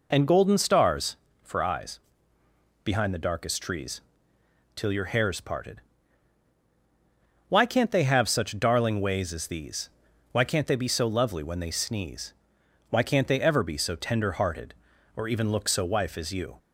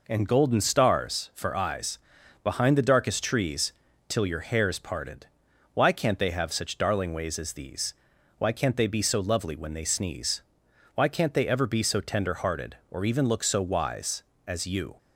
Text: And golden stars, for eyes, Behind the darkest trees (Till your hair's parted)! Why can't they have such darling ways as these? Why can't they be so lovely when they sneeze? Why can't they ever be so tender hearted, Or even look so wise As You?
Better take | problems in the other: second | says "wife" for "wise"; at 15.8 s

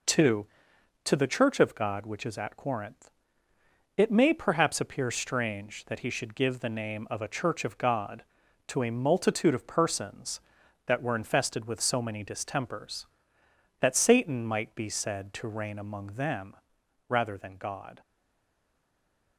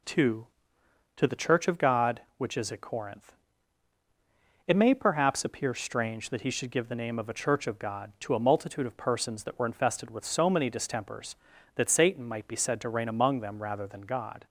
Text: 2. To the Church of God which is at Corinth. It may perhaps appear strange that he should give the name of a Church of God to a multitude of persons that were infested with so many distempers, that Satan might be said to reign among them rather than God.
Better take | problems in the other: second | pauses between "them" and "rather"; noticeable; at 16.5 s; 0.54 s long // stays silent after the last word; noticeable; from 18.0 s on; 1.3 s long

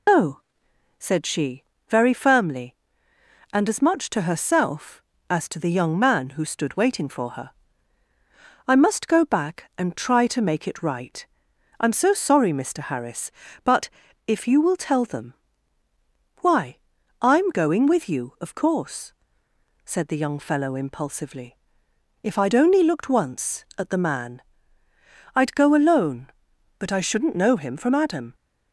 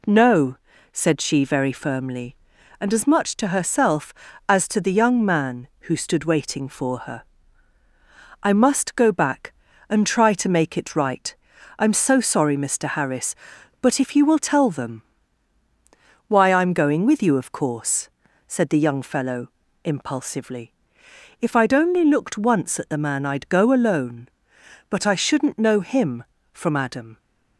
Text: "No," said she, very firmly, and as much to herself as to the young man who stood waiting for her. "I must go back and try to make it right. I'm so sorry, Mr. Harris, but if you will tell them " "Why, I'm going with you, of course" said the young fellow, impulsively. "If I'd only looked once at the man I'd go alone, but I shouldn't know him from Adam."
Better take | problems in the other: second | loses the start of "No"; at 0.0 s; 110 ms // pauses between "but" and "if"; at 13.8 s; 0.38 s long // pauses between "course" and "said"; noticeable; at 19.1 s; 0.72 s long; also in the second // pauses between "man" and "I'd"; noticeable; at 24.4 s; 0.94 s long

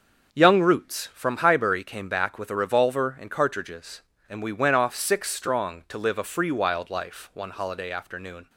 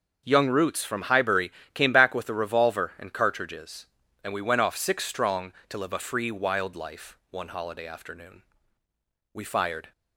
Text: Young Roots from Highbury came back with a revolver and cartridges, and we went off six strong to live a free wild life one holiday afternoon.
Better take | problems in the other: first | starts louder than the rest; until 1.2 s; 6.5 dB; also in the first // pauses between "Highbury" and "came"; slight; at 1.5 s; 0.22 s long // goes on to say "We fired"; from 9.3 s on; 0.58 s long

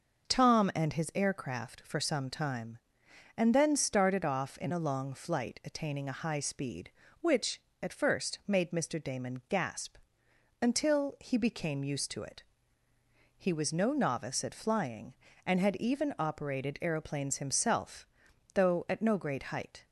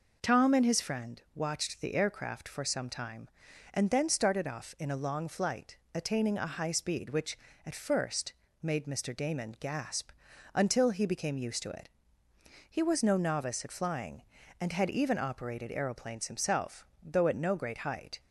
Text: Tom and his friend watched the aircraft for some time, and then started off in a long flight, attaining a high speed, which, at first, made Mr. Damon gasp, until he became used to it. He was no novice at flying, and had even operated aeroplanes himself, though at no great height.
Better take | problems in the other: second | skips "friend watched the"; at 1.1 s

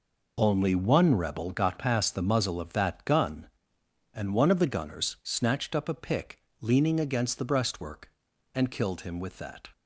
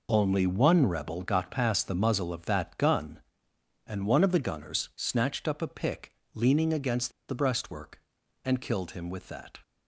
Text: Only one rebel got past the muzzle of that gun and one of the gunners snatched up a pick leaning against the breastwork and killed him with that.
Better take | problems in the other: first | pauses between "pick" and "leaning"; slight; at 6.1 s; 0.20 s long; slight in the first // pauses between "against" and "the"; slight; at 7.1 s; 0.17 s long

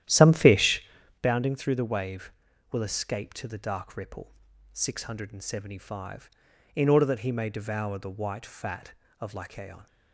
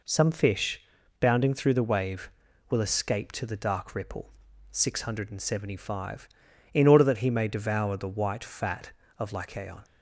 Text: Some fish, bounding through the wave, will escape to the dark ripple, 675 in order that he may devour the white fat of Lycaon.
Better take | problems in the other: second | starts louder than the rest; strong; until 1.3 s; 11.5 dB

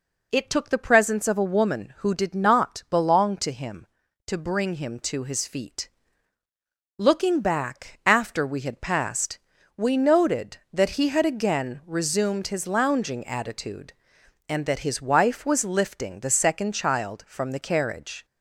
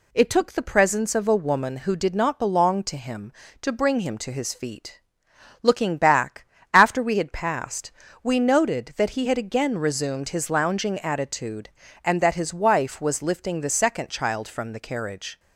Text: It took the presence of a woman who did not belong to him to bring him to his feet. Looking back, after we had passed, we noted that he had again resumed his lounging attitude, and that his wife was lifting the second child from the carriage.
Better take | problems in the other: neither | none

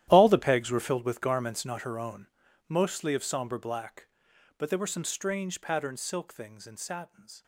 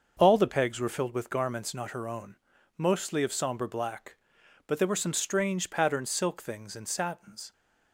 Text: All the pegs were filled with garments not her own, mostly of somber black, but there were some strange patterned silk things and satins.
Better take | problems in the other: second | gets quieter; strong; throughout; 16 dB // starts louder than the rest; strong; until 1.0 s; 12.5 dB; also in the second

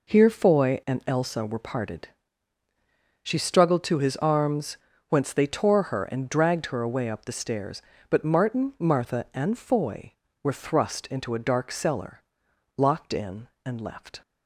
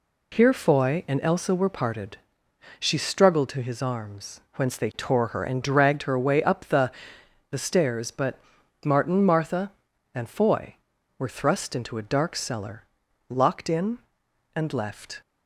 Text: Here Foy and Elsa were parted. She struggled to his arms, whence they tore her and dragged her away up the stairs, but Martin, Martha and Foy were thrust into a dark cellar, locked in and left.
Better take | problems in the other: first | says "the" twice; at 7.5 s // pauses between "but" and "Martin"; noticeable; at 8.3 s; 0.48 s long

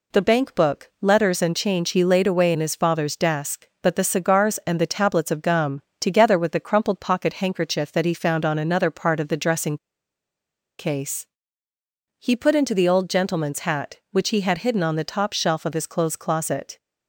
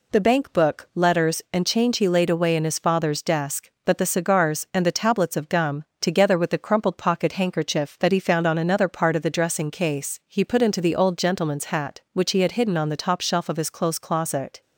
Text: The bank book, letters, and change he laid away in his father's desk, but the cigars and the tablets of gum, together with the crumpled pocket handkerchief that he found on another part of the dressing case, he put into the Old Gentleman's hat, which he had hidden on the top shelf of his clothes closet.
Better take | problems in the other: second | pauses between "dressing" and "case"; at 9.7 s; 1.0 s long

